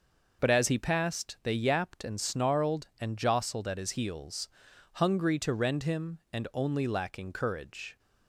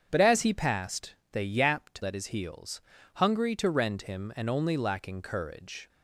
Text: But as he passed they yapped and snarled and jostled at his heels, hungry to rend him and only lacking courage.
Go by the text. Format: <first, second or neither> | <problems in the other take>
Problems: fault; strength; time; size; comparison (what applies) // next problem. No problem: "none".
first | starts louder than the rest; strong; until 1.1 s; 8 dB // pauses between "passed" and "they"; slight; at 1.1 s; 0.20 s long // skips "and snarled and jostled"; at 2.0 s